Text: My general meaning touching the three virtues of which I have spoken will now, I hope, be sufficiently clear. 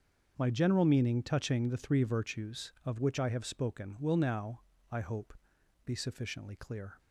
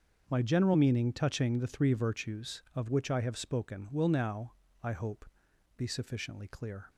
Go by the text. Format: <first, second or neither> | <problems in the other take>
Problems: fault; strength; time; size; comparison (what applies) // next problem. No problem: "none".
neither | starts louder than the rest; the same in both